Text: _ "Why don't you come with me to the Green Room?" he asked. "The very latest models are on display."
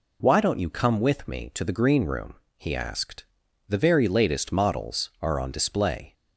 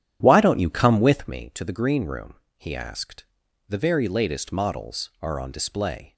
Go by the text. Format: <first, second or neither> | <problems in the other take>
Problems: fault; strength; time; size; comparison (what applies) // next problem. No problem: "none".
first | starts louder than the rest; strong; until 1.4 s; 10.5 dB